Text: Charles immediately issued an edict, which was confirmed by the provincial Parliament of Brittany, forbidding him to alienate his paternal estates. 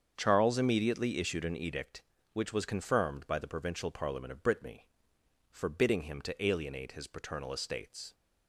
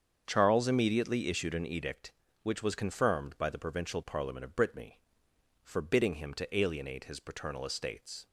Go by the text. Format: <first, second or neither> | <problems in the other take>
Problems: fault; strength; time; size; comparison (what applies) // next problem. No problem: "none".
neither | starts louder than the rest; strong; the same in both